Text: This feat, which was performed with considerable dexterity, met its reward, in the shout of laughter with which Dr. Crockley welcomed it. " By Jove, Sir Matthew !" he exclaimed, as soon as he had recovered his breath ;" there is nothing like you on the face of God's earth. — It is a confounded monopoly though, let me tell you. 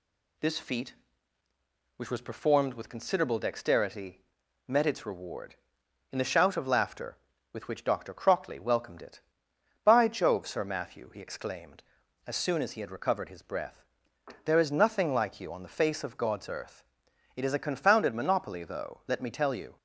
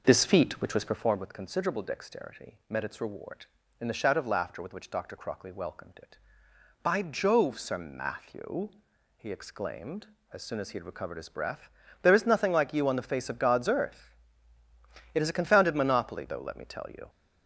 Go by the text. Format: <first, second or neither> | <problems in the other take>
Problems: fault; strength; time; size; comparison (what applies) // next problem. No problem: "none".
first | starts louder than the rest; noticeable; until 1.2 s; 5 dB